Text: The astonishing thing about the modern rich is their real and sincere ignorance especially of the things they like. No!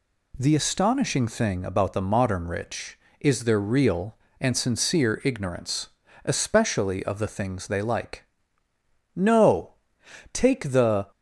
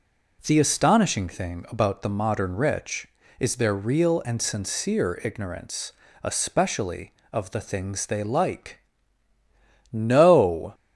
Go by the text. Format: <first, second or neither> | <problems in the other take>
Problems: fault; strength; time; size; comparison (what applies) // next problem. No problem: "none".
second | pauses between "ignorance" and "especially"; at 5.8 s; 0.40 s long; slight in the second // goes on to say "Take the"; noticeable; from 10.3 s on; 0.72 s long